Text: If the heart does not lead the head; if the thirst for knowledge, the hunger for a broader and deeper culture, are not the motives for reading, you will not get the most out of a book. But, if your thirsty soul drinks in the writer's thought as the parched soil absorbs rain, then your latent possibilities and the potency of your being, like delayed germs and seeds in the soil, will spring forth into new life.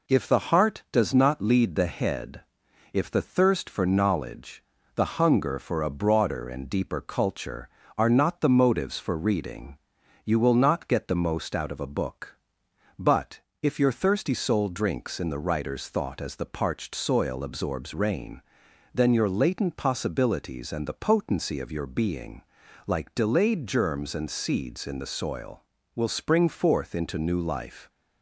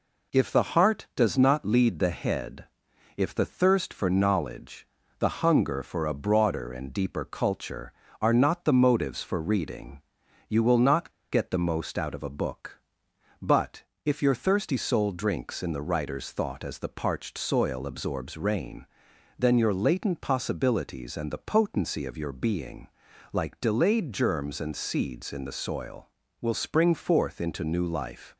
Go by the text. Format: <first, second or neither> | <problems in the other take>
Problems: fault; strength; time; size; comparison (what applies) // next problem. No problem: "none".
first | pauses between "not" and "get"; slight; at 11.0 s; 0.21 s long